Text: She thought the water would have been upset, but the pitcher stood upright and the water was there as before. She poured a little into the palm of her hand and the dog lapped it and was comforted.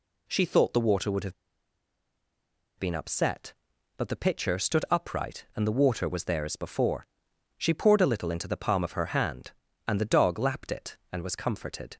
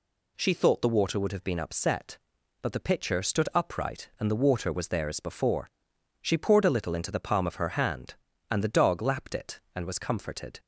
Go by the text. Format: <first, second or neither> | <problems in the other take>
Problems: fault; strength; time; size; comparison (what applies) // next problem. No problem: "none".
second | pauses between "have" and "been"; strong; at 1.3 s; 1.4 s long